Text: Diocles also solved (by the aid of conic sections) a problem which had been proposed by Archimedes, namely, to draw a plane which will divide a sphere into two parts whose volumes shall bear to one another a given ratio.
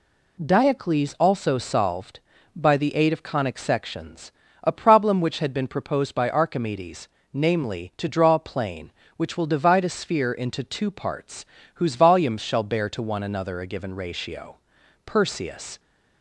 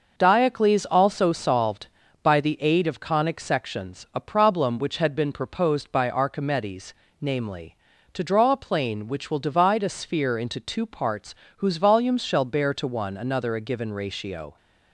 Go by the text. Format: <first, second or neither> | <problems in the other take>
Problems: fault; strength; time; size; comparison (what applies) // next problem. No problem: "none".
second | pauses between "parts" and "whose"; slight; at 11.4 s; 0.32 s long; slight in the second // goes on to say "Perseus"; noticeable; from 15.0 s on; 0.74 s long